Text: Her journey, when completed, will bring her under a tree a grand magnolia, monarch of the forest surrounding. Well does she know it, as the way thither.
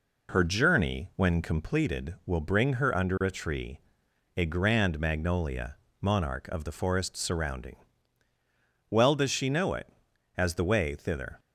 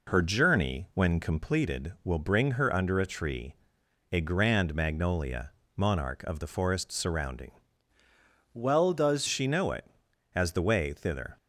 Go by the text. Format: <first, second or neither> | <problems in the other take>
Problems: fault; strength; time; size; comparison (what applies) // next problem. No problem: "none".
first | pauses between "tree" and "a"; noticeable; at 3.5 s; 0.54 s long; noticeable in the first // changes voice from "Well" to "does"; from 8.5 to 9.2 s; 0.7 s long